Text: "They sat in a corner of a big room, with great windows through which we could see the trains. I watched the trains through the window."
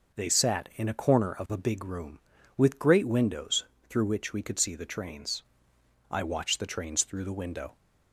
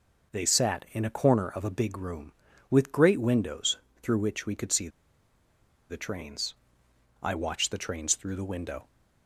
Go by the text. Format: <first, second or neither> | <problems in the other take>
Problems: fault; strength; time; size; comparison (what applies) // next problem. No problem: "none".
first | pauses between "windows" and "through"; slight; at 3.7 s; 0.24 s long; slight in the first // pauses between "see" and "the"; at 4.8 s; 1.0 s long